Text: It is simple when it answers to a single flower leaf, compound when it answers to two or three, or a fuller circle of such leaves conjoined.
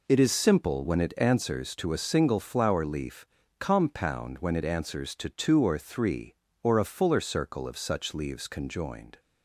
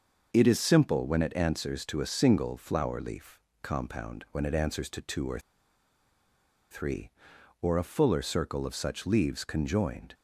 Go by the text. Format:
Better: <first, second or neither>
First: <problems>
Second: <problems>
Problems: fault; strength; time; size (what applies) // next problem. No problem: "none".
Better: first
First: none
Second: starts louder than the rest; noticeable; until 1.3 s; 6 dB // pauses between "or" and "three"; strong; at 5.3 s; 1.3 s long